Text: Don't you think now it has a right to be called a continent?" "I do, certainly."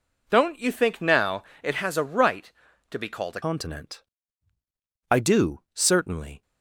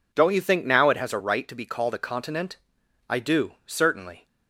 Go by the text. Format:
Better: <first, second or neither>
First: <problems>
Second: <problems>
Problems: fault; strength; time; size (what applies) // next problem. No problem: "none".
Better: second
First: pauses between "now" and "it"; slight; at 1.4 s; 0.20 s long // changes voice at "continent"; from 3.4 s on; 3.0 s long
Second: none